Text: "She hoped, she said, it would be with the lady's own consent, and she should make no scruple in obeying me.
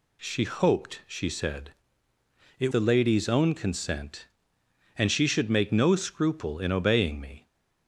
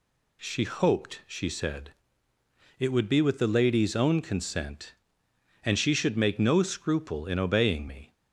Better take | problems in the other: second | skips "would be with"; at 2.7 s

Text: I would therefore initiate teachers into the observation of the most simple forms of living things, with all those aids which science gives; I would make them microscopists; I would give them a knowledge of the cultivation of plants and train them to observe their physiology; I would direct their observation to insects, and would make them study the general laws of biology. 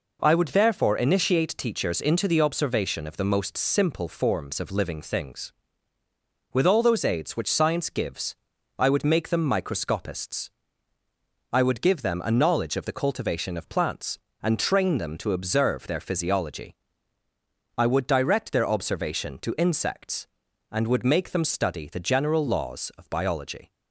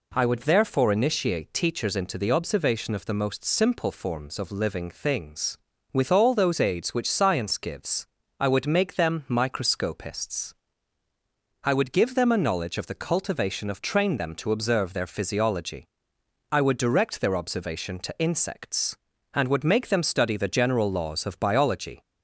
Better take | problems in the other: first | skips "plants and"; at 13.8 s

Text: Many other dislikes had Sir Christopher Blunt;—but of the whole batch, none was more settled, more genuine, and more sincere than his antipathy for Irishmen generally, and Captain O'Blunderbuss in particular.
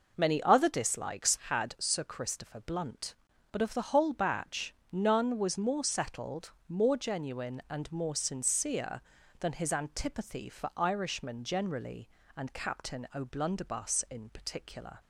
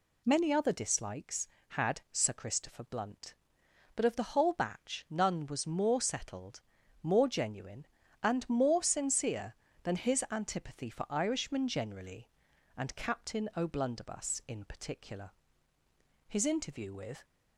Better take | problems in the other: first | goes on to say "His interview with"; noticeable; from 16.2 s on; 0.96 s long

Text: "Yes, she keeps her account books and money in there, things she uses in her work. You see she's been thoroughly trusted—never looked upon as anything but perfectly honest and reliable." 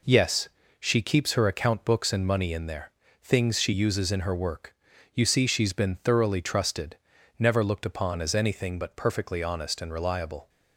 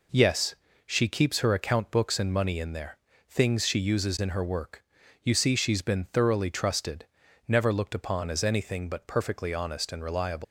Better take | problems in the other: first | leaves "reliable" unfinished; at 10.4 s; 150 ms

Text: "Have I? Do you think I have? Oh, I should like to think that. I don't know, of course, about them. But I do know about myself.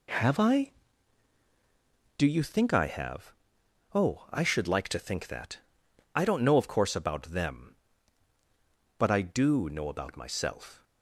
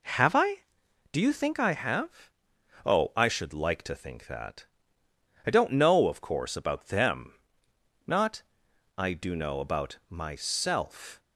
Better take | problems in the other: first | says "Not" for "But"; at 8.0 s

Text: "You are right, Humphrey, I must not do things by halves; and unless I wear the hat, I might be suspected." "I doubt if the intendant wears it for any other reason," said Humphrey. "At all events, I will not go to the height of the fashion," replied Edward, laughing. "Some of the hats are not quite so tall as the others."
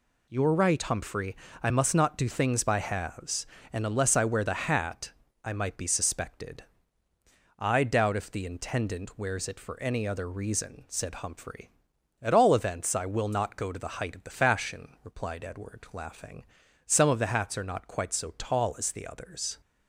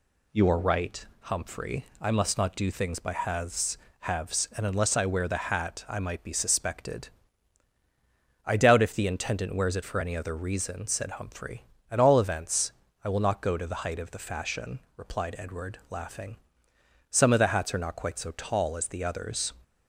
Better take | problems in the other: first | says "halves" twice; at 4.0 s

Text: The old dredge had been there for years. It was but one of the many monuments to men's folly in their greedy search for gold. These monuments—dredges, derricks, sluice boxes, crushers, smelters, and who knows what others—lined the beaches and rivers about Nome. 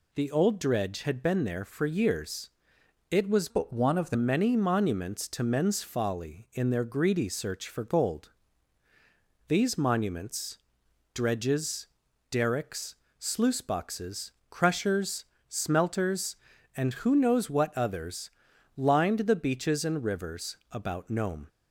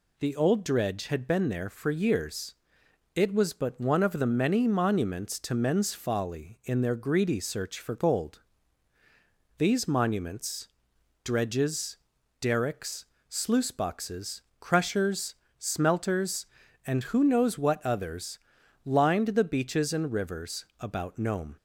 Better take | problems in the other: second | changes voice from "but" to "the"; from 3.4 to 4.1 s; 0.7 s long

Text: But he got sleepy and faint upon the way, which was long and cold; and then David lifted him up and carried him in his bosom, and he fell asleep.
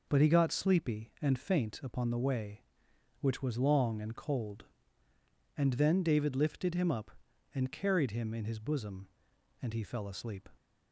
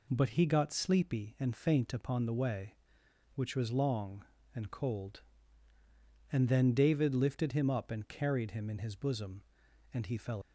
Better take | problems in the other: first | stops before "asleep"; at 10.4 s

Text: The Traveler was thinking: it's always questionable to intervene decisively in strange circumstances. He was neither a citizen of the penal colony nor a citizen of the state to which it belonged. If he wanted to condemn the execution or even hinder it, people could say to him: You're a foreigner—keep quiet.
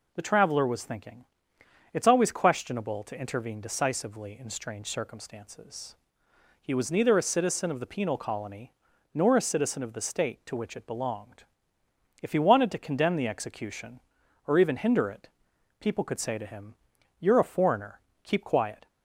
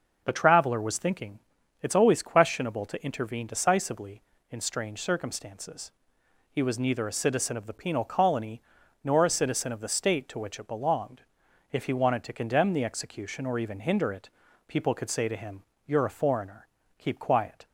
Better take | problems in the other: neither | pauses between "colony" and "nor"; the same in both

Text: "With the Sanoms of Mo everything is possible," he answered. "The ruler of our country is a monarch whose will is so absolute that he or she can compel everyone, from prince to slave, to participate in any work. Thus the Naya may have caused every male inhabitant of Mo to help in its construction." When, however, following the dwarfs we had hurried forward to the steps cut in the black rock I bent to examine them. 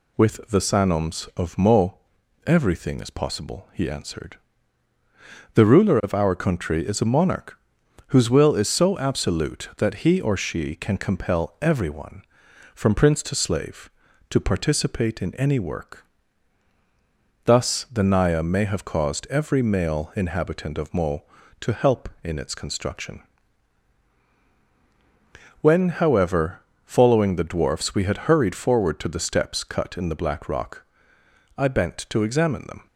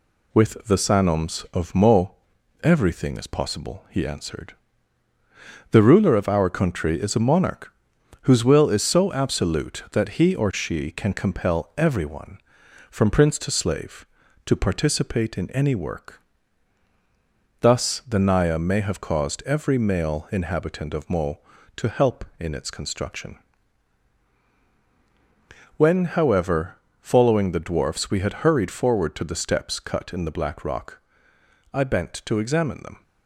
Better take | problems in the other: first | gets quieter; throughout; 3.5 dB // pauses between "Mo" and "everything"; noticeable; at 2.1 s; 0.48 s long; noticeable in the first // pauses between "monarch" and "whose"; noticeable; at 7.6 s; 0.54 s long; noticeable in the first // pauses between "rock" and "I"; noticeable; at 31.0 s; 0.74 s long; noticeable in the first

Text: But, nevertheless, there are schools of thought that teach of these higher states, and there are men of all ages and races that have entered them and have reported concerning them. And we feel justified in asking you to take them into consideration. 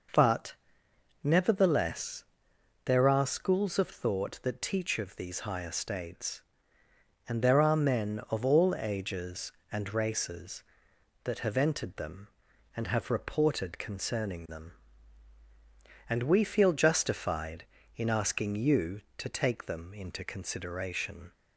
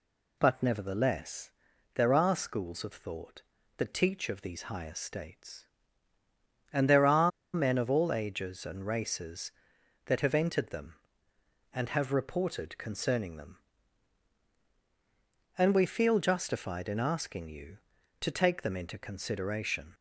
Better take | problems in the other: first | pauses between "are" and "men"; slight; at 7.3 s; 0.23 s long

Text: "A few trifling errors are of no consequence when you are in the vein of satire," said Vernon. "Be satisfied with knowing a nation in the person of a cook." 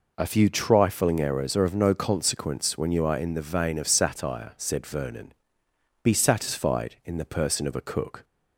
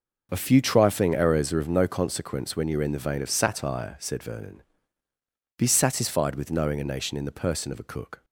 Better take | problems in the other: second | skips "with knowing a nation"; at 7.0 s

